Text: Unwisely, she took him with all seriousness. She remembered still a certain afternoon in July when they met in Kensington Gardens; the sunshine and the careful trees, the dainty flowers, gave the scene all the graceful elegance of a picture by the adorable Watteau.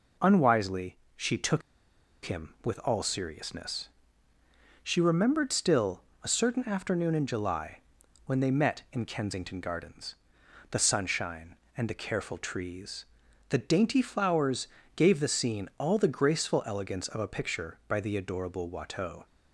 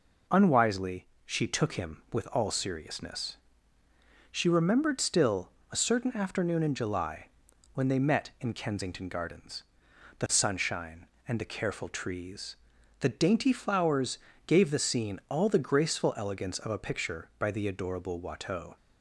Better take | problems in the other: second | pauses between "took" and "him"; noticeable; at 1.6 s; 0.63 s long // pauses between "still" and "a"; slight; at 6.0 s; 0.20 s long; slight in the second // pauses between "July" and "when"; noticeable; at 7.7 s; 0.48 s long; noticeable in the second

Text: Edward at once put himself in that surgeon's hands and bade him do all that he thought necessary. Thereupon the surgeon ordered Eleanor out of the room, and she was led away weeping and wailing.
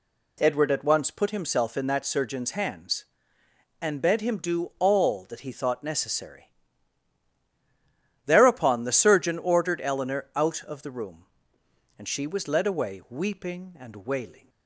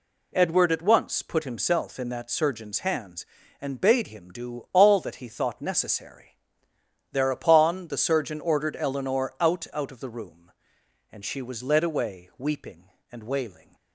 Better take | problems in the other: first | says "out" twice; at 9.7 s

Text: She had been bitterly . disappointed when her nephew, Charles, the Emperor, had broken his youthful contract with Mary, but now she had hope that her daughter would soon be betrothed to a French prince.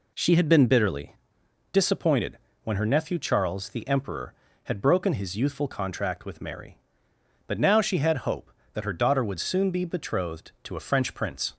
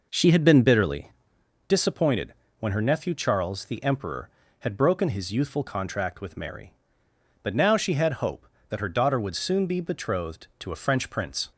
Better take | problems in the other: first | starts louder than the rest; noticeable; until 1.4 s; 5 dB // pauses between "disappointed" and "when"; slight; at 2.3 s; 0.26 s long; slight in the first

